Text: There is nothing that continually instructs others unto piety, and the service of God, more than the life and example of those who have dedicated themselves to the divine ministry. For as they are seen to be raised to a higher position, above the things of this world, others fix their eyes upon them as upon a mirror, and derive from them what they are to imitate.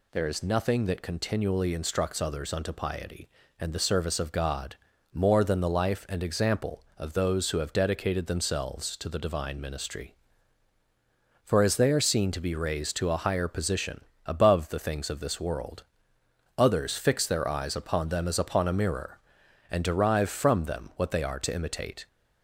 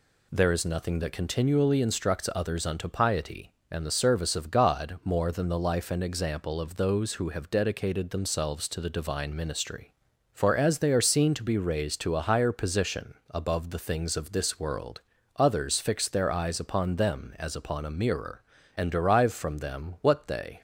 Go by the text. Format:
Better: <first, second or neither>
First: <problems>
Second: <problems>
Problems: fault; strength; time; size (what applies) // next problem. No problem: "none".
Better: first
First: none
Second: stops before "are to imitate"; at 20.5 s